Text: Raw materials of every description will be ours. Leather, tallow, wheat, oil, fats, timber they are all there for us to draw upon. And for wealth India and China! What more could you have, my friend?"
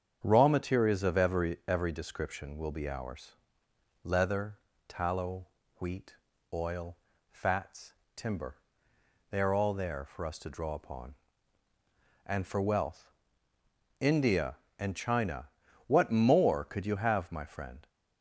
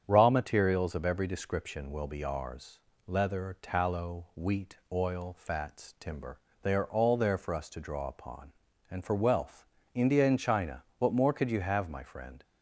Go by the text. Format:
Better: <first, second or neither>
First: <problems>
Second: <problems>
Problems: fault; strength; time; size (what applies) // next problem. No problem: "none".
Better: second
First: starts louder than the rest; strong; until 1.2 s; 8 dB // says "every" twice; at 1.6 s // pauses between "timber" and "they"; noticeable; at 8.5 s; 0.74 s long // pauses between "wealth" and "India"; noticeable; at 13.1 s; 0.88 s long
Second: starts louder than the rest; strong; until 1.0 s; 8 dB // pauses between "timber" and "they"; slight; at 6.4 s; 0.22 s long // pauses between "wealth" and "India"; slight; at 9.6 s; 0.30 s long